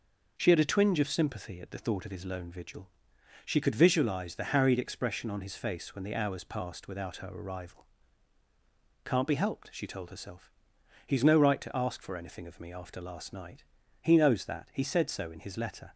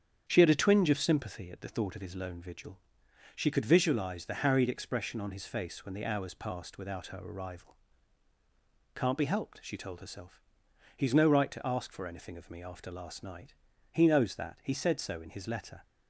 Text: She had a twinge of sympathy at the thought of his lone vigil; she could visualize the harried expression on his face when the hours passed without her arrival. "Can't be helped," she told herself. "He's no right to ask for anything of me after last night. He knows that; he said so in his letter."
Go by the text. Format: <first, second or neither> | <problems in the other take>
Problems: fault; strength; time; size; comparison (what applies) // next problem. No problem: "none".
first | starts louder than the rest; strong; until 1.5 s; 8 dB